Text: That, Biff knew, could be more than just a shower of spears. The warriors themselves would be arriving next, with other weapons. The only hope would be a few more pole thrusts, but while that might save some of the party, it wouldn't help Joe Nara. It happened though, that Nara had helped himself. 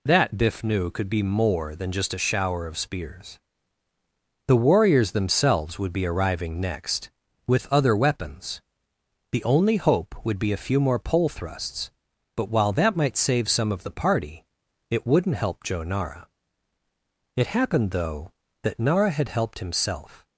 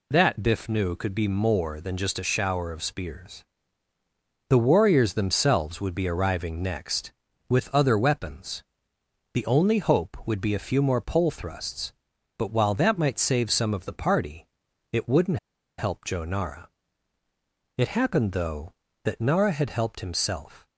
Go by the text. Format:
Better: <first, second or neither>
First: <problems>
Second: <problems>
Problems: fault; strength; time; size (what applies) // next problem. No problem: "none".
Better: first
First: none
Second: pauses between "wouldn't" and "help"; at 15.3 s; 0.40 s long